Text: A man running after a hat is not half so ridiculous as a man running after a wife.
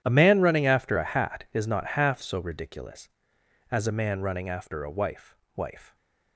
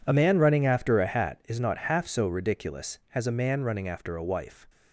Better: second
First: says "wife" twice; at 5.5 s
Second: none

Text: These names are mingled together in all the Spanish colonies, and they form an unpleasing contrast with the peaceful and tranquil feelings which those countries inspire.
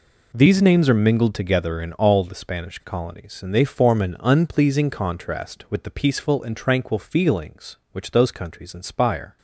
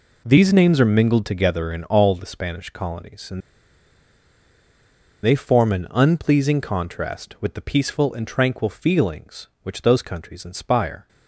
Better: first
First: none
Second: pauses between "and" and "they"; strong; at 3.4 s; 1.8 s long

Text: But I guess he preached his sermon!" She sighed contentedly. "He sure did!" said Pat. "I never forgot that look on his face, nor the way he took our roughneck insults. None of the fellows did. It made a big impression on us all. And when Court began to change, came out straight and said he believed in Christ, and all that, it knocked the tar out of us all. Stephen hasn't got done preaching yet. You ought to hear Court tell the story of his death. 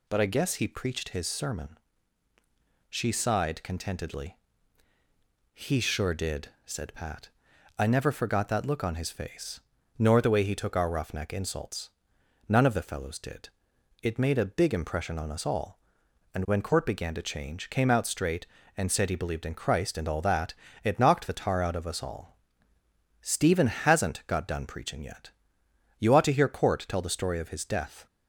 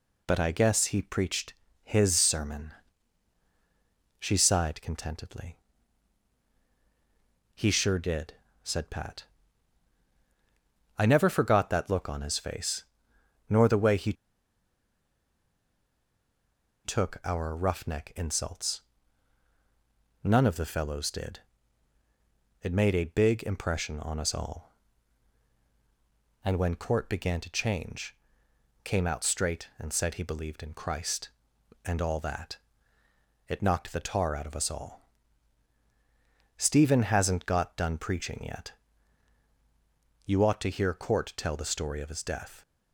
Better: first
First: none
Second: pauses between "preached" and "his"; slight; at 1.5 s; 0.30 s long // pauses between "he" and "took"; strong; at 14.1 s; 2.7 s long

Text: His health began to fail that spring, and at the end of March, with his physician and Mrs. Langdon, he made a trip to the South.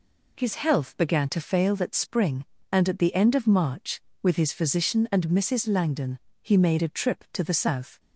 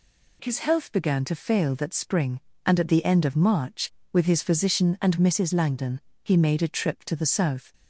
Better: neither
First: none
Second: none

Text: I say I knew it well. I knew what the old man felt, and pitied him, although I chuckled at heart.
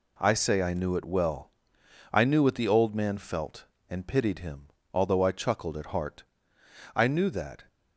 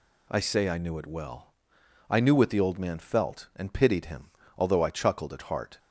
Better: second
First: goes on to say "I knew that"; noticeable; from 6.9 s on; 0.70 s long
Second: none

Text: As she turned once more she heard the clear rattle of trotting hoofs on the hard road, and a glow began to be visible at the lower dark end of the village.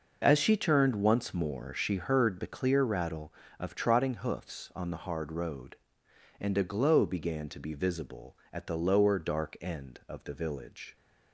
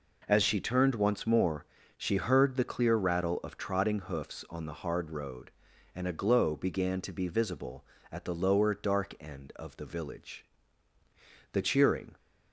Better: first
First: none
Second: pauses between "more" and "she"; slight; at 1.6 s; 0.32 s long // goes on to say "The cheering"; noticeable; from 11.5 s on; 0.64 s long

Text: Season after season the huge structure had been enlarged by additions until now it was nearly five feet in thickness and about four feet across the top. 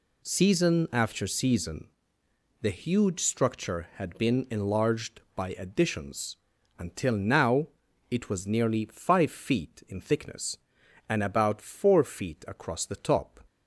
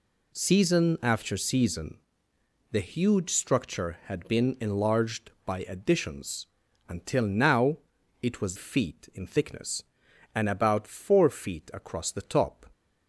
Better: first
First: pauses between "season" and "the"; noticeable; at 1.8 s; 0.74 s long // pauses between "additions" and "until"; at 6.3 s; 0.42 s long // pauses between "now" and "it"; at 7.6 s; 0.40 s long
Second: pauses between "season" and "the"; noticeable; at 1.9 s; 0.74 s long // pauses between "additions" and "until"; at 6.4 s; 0.42 s long // pauses between "now" and "it"; at 7.7 s; 0.42 s long // skips "nearly five"; at 8.5 s

